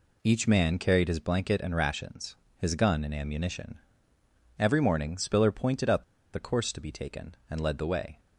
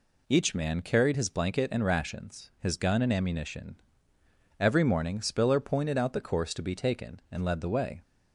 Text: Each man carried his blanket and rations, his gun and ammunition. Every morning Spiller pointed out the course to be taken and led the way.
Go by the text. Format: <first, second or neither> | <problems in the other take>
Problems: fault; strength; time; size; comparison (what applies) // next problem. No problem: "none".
second | pauses between "out" and "the"; slight; at 6.0 s; 0.29 s long